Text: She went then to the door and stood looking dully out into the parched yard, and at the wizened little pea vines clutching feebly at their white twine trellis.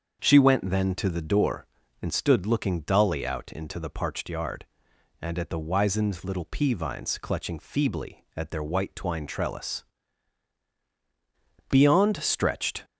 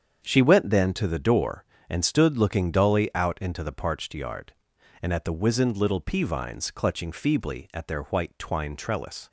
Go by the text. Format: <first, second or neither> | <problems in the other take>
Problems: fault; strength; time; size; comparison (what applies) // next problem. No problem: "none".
second | starts louder than the rest; until 1.2 s; 7 dB; strong in the second // goes on to say "Beyond stretched"; noticeable; from 11.7 s on; 1.1 s long